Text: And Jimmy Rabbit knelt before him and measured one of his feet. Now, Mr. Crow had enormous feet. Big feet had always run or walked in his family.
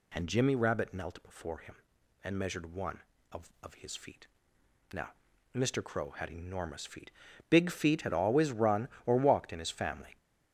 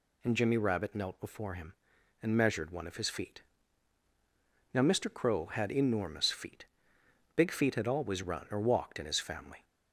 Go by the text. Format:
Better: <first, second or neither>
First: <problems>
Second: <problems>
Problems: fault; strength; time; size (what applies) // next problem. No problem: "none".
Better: second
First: says "of" twice; at 3.6 s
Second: none